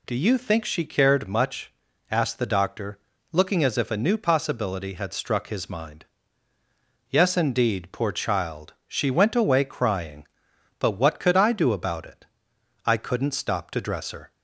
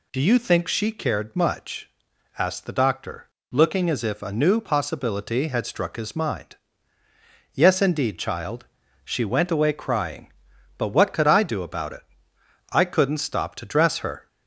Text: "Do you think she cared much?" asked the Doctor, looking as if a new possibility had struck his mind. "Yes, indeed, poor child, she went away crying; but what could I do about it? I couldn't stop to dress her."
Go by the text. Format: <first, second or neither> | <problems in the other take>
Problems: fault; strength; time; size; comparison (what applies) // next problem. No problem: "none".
first | skips "poor"; at 8.1 s